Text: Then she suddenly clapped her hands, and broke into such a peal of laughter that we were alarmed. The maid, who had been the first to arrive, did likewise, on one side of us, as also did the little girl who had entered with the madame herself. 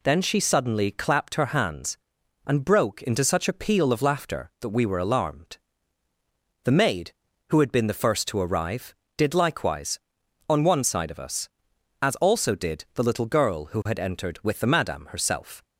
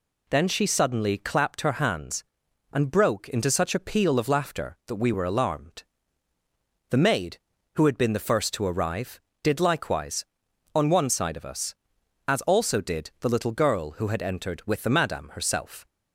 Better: neither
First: none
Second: none

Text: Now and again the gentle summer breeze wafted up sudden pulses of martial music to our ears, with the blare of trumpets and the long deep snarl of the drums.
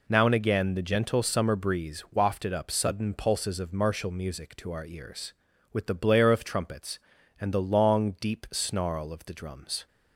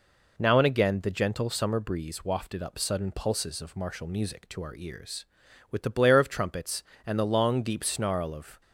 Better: first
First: none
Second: stops before "the drums"; at 8.6 s

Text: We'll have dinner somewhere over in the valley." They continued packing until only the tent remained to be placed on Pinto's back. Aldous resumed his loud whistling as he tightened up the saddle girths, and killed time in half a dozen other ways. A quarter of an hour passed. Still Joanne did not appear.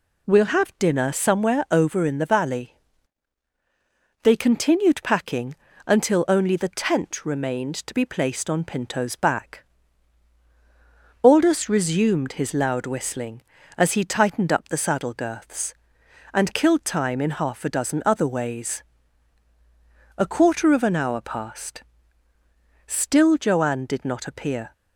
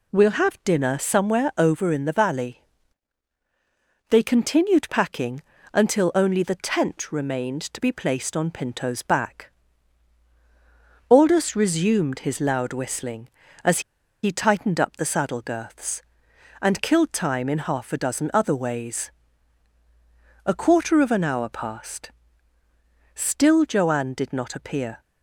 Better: first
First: pauses between "packing" and "until"; slight; at 5.5 s; 0.32 s long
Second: pauses between "packing" and "until"; slight; at 5.3 s; 0.32 s long // pauses between "as" and "he"; at 13.7 s; 0.43 s long

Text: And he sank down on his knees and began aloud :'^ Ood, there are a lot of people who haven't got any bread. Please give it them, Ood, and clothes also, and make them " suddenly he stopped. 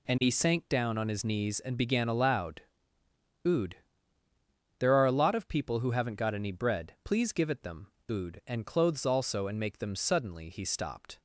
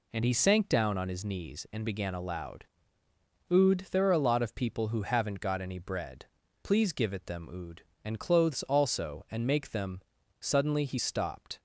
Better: neither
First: none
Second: none

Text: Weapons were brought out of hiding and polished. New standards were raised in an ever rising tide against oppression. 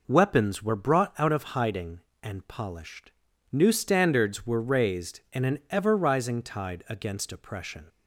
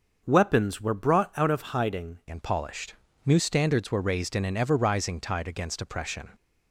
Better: first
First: none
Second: starts louder than the rest; until 1.2 s; 6.5 dB // changes voice at "and"; from 2.2 s on; 4.1 s long

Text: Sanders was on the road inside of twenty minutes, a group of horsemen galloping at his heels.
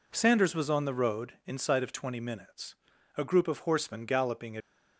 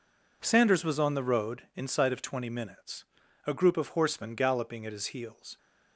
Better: second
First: stops before "at his heels"; at 4.6 s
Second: none

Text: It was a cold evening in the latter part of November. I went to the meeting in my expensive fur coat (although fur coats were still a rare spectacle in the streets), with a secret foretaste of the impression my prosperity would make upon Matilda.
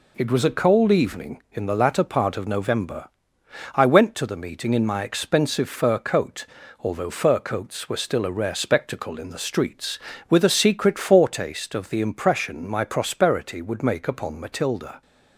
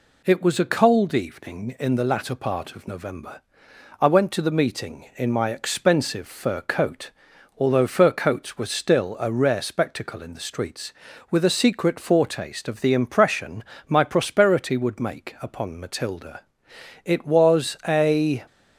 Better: first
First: none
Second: pauses between "impression" and "my"; slight; at 13.6 s; 0.24 s long // goes on to say "It was a"; from 17.0 s on; 1.4 s long

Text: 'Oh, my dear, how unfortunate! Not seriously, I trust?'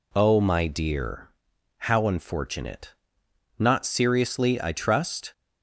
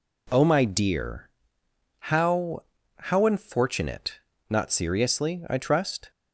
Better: first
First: none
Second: says "how" twice; at 2.9 s

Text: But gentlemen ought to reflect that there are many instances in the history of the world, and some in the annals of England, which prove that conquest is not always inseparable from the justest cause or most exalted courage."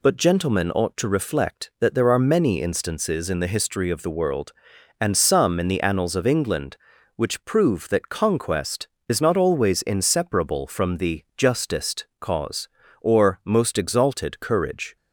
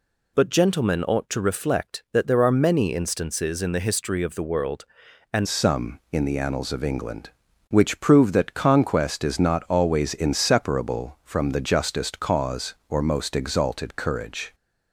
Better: first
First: none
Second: changes voice at "some"; from 5.4 s on; 9.1 s long

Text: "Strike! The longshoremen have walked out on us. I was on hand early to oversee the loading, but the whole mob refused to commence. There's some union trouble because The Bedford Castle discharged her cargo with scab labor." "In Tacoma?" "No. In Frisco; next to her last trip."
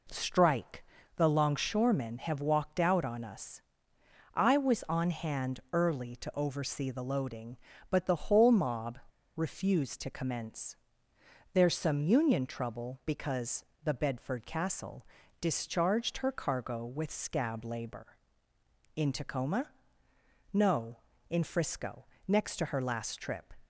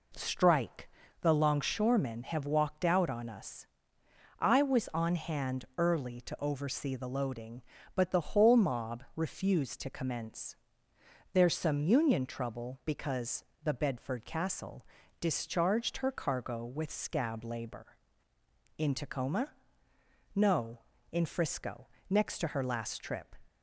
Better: second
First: pauses between "mob" and "refused"; slight; at 8.9 s; 0.35 s long // pauses between "because" and "The"; slight; at 13.6 s; 0.20 s long // pauses between "Castle" and "discharged"; slight; at 15.0 s; 0.36 s long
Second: pauses between "because" and "The"; slight; at 13.4 s; 0.20 s long // pauses between "Castle" and "discharged"; slight; at 14.8 s; 0.36 s long

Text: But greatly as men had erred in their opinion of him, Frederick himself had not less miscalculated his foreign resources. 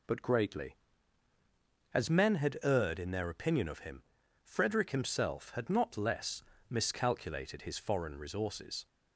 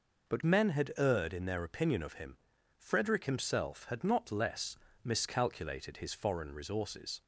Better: first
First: pauses between "less" and "miscalculated"; slight; at 6.4 s; 0.26 s long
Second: skips "greatly as"; at 0.4 s // pauses between "less" and "miscalculated"; slight; at 4.7 s; 0.26 s long

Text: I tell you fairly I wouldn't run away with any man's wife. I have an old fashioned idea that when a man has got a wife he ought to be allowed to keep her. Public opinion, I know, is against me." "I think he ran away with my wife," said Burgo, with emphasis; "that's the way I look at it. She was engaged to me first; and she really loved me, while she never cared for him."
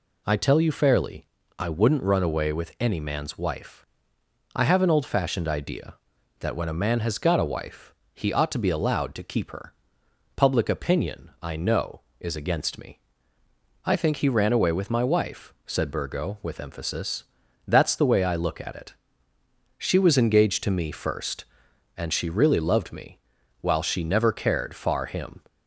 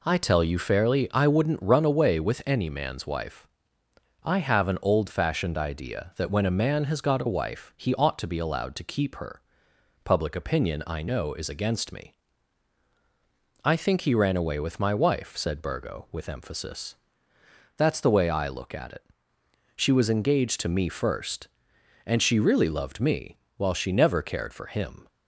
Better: second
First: pauses between "fairly" and "I"; slight; at 1.2 s; 0.32 s long // pauses between "wife" and "he"; slight; at 7.9 s; 0.20 s long // says "far" for "for"; at 24.7 s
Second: none

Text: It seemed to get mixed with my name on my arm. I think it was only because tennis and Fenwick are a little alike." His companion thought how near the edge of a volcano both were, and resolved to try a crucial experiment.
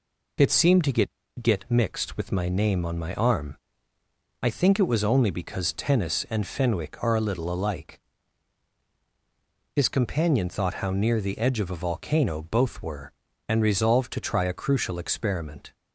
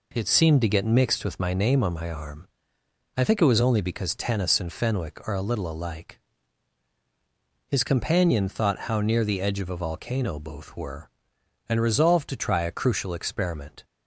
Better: second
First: says "get" twice; at 1.4 s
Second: none

